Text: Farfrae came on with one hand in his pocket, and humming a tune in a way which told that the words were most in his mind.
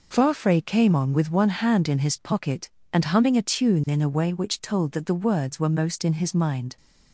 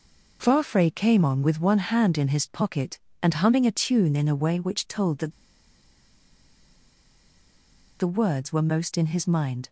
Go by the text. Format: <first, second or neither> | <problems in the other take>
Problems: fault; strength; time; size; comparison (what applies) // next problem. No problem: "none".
first | pauses between "that" and "the"; strong; at 5.3 s; 2.6 s long